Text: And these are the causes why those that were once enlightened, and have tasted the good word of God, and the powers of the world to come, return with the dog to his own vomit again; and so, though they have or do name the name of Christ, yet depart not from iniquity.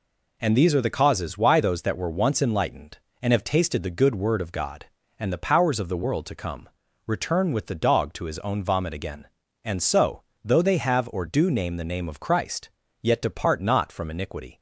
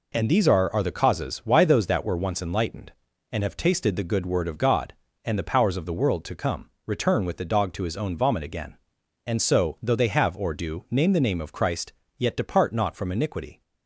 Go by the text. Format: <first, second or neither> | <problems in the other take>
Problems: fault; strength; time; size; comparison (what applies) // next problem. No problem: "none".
first | says "are" twice; at 0.7 s